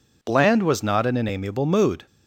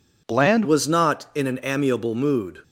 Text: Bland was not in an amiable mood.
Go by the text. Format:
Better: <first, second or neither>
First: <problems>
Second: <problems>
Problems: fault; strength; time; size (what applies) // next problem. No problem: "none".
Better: first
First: none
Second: changes voice at "was"; from 0.6 s on; 2.0 s long